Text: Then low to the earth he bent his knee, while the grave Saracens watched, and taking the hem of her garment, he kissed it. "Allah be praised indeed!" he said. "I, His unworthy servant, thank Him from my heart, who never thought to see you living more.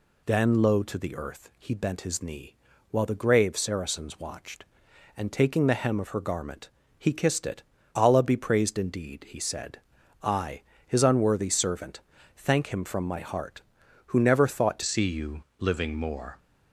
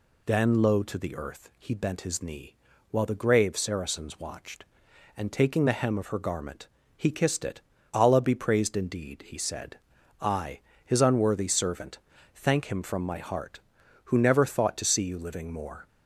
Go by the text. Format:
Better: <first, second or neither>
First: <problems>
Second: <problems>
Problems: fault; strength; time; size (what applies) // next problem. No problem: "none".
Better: second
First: changes voice at "see"; from 14.8 s on; 1.5 s long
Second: none